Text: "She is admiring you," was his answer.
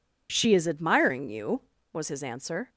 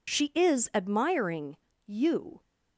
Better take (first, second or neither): first